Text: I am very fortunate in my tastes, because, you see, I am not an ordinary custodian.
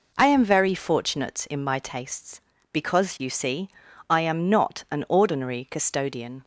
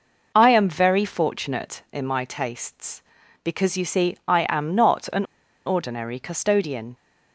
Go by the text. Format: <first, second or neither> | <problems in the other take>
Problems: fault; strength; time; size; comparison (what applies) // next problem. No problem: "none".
first | pauses between "an" and "ordinary"; at 5.2 s; 0.41 s long